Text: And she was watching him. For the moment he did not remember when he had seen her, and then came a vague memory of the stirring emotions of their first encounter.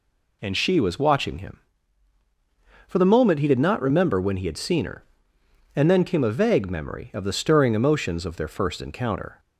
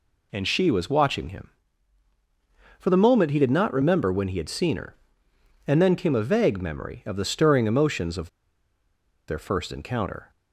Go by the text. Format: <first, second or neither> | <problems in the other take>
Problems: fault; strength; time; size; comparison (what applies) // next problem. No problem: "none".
first | pauses between "of" and "their"; at 8.2 s; 1.0 s long